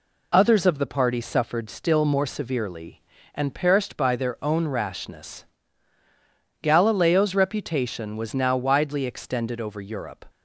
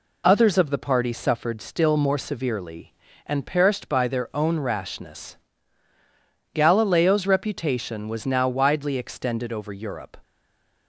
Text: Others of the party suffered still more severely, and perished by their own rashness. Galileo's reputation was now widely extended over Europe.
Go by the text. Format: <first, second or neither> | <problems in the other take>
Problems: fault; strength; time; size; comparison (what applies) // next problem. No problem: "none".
first | stays silent after the last word; slight; from 10.2 s on; 0.6 s long